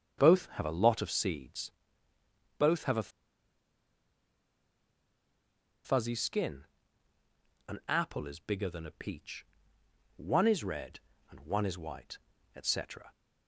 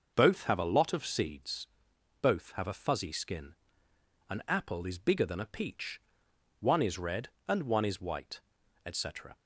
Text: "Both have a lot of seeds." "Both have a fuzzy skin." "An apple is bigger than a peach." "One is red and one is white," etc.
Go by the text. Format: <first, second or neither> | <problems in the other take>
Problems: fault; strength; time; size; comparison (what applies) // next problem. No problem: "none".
second | starts louder than the rest; until 1.2 s; 7 dB // pauses between "a" and "fuzzy"; strong; at 3.0 s; 2.7 s long